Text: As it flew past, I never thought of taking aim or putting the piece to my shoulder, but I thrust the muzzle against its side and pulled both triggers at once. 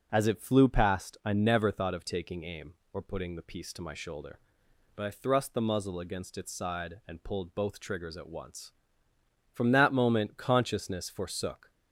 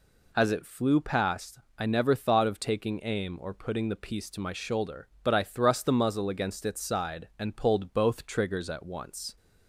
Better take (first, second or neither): second